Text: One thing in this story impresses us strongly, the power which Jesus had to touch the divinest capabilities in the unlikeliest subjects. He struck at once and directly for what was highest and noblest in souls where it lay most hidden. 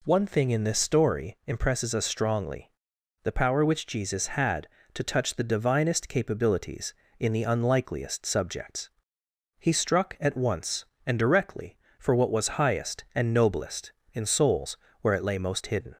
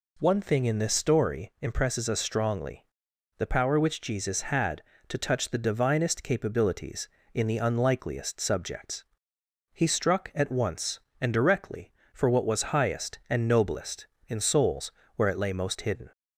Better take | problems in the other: neither | pauses between "souls" and "where"; slight; the same in both

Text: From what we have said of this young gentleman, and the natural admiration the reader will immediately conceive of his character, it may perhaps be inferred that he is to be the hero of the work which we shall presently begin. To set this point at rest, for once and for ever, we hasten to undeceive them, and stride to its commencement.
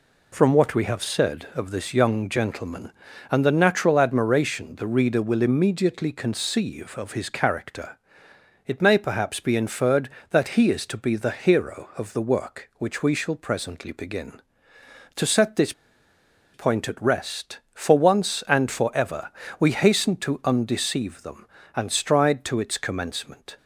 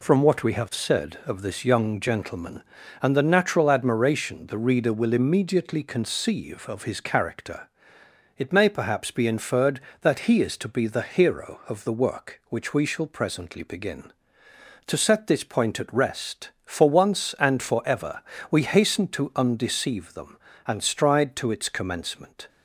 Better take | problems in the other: second | pauses between "this" and "point"; noticeable; at 15.7 s; 0.82 s long

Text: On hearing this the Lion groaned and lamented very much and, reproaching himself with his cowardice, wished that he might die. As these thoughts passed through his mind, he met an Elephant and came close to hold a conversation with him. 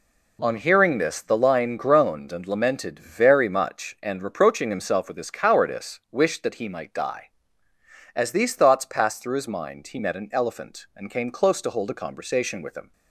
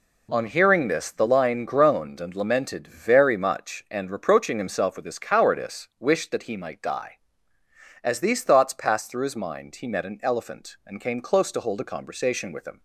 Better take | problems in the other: neither | none

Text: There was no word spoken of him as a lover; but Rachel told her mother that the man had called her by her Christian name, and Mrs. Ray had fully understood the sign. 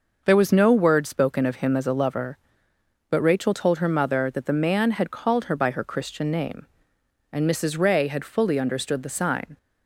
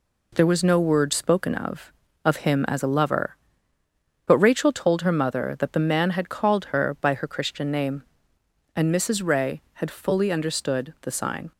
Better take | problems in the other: first | says "of" twice; at 2.2 s

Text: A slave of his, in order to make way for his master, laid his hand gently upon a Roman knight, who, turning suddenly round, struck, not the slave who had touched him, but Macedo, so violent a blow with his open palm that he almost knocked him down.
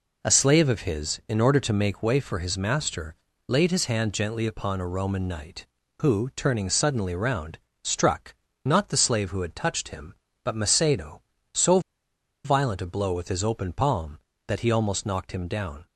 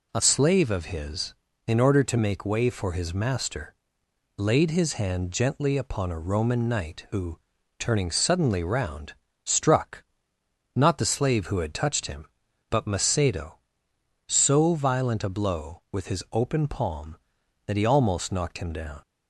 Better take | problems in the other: second | pauses between "so" and "violent"; noticeable; at 11.7 s; 0.65 s long

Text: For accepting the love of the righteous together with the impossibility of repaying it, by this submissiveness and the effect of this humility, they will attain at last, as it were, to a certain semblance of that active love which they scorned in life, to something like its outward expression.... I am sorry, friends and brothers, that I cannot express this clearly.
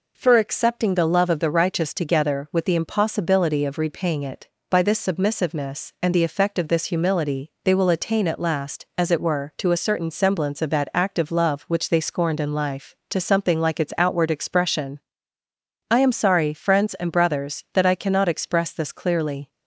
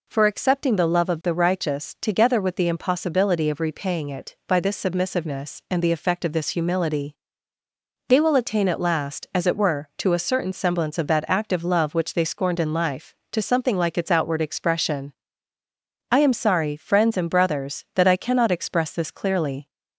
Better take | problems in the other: neither | none

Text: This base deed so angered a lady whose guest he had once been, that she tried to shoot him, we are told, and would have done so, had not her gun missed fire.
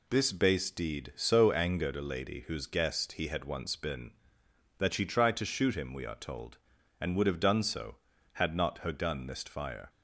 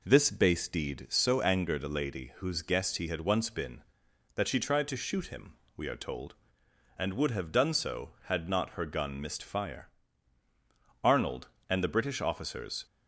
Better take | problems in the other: first | goes on to say "Arnold and the British officers"; strong; from 11.0 s on; 1.8 s long

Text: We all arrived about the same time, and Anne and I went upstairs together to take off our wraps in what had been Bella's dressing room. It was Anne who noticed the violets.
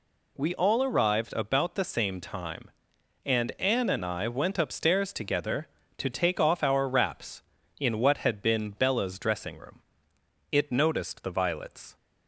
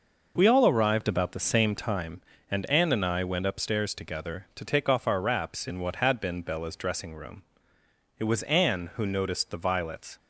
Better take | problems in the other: second | skips "was Anne who"; at 10.7 s

